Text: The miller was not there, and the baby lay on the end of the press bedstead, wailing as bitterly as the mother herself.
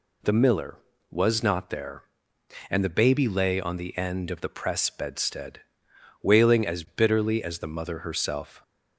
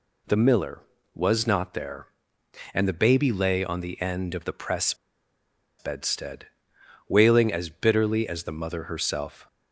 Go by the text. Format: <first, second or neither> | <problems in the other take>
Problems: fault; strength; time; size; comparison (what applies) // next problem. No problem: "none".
first | pauses between "press" and "bedstead"; noticeable; at 4.9 s; 0.84 s long